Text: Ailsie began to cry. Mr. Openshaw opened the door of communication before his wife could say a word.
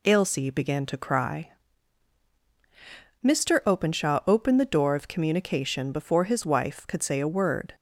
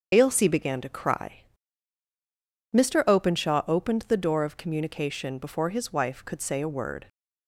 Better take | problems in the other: first | loses the start of "Ailsie"; at 0.1 s; 45 ms // starts louder than the rest; strong; until 1.1 s; 7.5 dB

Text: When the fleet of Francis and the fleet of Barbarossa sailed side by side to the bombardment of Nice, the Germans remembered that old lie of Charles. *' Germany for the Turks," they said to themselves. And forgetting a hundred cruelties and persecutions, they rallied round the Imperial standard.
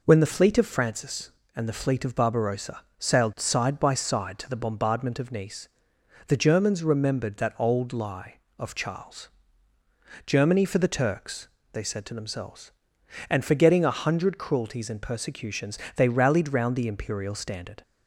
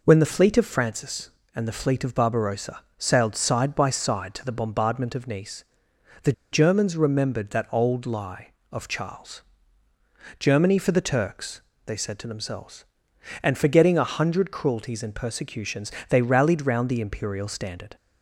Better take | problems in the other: first | pauses between "Barbarossa" and "sailed"; slight; at 2.7 s; 0.18 s long; slight in the first // pauses between "the" and "Germans"; slight; at 6.3 s; 0.20 s long

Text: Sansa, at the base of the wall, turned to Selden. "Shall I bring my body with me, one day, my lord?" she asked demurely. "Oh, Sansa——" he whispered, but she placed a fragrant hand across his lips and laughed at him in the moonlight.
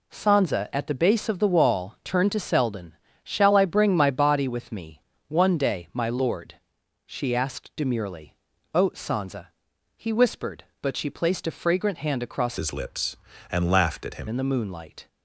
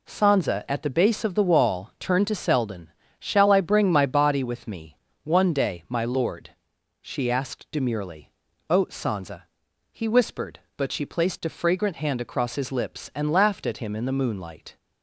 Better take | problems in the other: second | changes voice from "his" to "him"; from 12.5 to 14.2 s; 1.7 s long

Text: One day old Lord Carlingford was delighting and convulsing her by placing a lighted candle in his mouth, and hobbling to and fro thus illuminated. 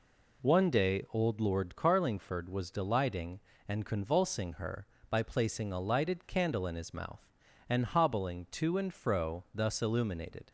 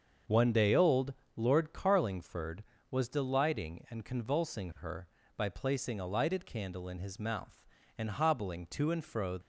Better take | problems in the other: first | starts louder than the rest; until 1.5 s; 6.5 dB // pauses between "old" and "Lord"; slight; at 1.1 s; 0.22 s long // stops before "thus illuminated"; at 9.4 s

